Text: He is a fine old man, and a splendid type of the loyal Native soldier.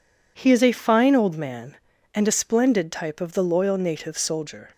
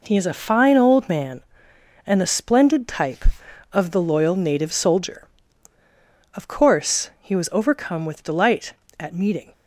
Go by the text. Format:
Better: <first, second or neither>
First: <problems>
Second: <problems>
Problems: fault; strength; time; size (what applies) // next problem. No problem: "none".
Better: first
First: none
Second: goes on to say "Of course he was overcome with delight at meeting"; strong; from 6.3 s on; 3.1 s long